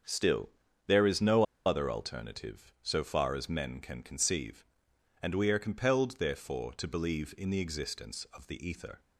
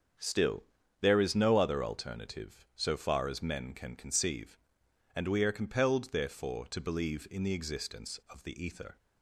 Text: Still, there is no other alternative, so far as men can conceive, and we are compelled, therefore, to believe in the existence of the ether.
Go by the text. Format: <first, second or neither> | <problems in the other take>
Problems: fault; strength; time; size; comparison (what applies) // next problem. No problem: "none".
second | starts louder than the rest; strong; until 1.4 s; 7 dB; strong in the second // pauses between "no" and "other"; slight; at 1.4 s; 0.22 s long